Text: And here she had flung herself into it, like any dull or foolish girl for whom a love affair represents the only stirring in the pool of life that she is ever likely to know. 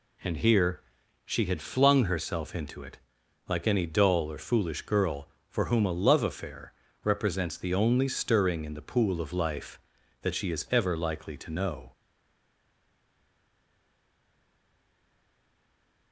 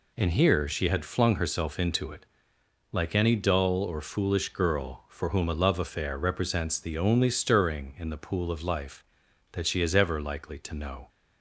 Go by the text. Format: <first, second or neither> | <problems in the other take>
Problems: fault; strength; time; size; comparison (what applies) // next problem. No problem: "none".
second | pauses between "here" and "she"; noticeable; at 0.8 s; 0.46 s long // pauses between "affair" and "represents"; slight; at 6.7 s; 0.32 s long // stays silent after the last word; strong; from 11.9 s on; 4.2 s long